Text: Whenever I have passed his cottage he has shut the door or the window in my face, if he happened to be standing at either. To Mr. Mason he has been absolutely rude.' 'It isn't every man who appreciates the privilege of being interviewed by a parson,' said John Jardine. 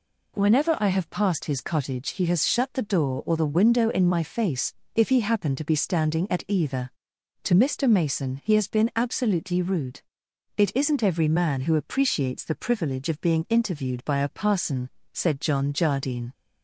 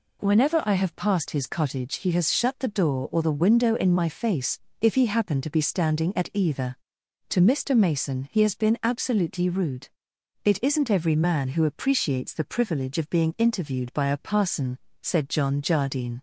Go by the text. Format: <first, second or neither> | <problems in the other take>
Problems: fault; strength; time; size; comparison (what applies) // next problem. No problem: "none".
neither | none